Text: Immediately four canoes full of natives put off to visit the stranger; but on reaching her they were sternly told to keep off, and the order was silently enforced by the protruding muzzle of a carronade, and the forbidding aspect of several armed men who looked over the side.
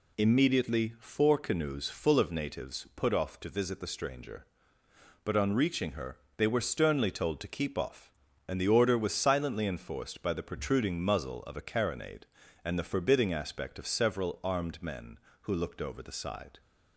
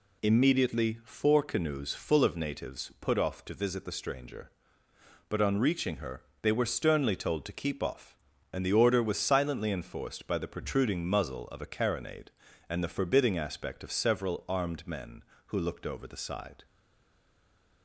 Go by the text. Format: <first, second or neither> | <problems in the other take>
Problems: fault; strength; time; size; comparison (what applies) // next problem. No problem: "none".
first | pauses between "her" and "they"; slight; at 6.2 s; 0.18 s long; slight in the first // stays silent after the last word; noticeable; from 16.6 s on; 1.2 s long